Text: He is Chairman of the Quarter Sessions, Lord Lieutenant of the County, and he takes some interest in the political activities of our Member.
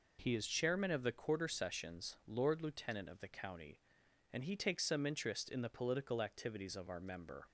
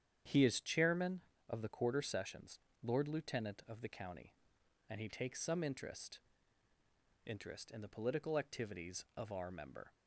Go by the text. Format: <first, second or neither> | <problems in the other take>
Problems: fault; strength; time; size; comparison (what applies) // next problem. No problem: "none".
first | starts louder than the rest; strong; until 1.5 s; 9 dB // says "interest" twice; at 7.2 s